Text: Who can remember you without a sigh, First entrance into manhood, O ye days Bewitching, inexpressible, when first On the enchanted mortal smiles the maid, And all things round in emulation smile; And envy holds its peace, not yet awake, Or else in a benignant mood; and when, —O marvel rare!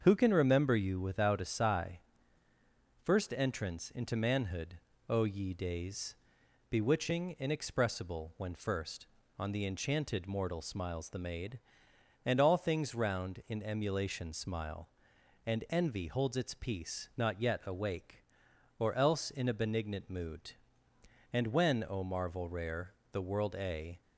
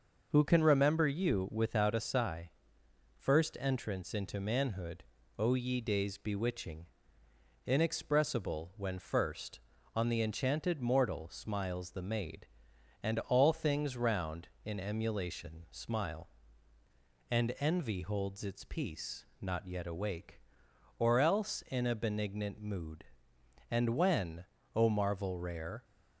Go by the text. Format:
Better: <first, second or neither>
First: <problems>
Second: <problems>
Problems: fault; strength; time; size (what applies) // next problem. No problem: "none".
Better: second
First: starts louder than the rest; until 1.0 s; 7 dB // pauses between "days" and "Bewitching"; noticeable; at 6.1 s; 0.56 s long // goes on to say "the world a"; noticeable; from 23.1 s on; 0.90 s long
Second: none